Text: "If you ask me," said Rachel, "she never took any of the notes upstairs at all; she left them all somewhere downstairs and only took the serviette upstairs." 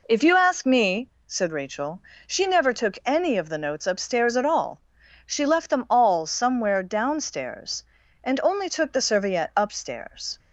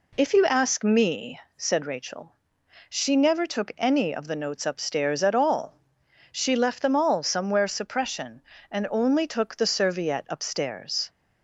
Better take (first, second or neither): first